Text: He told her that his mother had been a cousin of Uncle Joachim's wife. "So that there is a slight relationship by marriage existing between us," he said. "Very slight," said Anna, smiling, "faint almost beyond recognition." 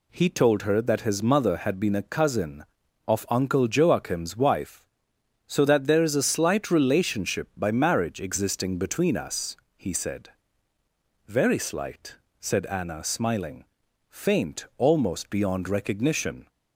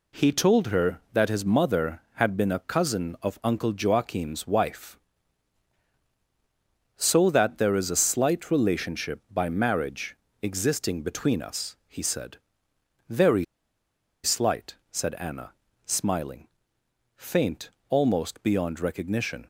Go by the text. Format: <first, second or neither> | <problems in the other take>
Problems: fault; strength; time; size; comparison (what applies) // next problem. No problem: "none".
first | pauses between "marriage" and "existing"; slight; at 10.1 s; 0.24 s long // pauses between "Very" and "slight"; noticeable; at 13.4 s; 0.79 s long // pauses between "faint" and "almost"; slight; at 17.7 s; 0.18 s long